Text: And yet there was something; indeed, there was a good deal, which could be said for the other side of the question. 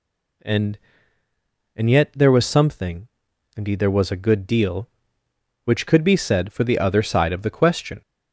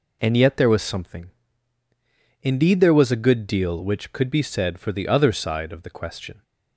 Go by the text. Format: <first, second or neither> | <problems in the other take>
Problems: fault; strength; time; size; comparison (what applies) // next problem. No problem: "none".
second | says "And" twice; at 1.7 s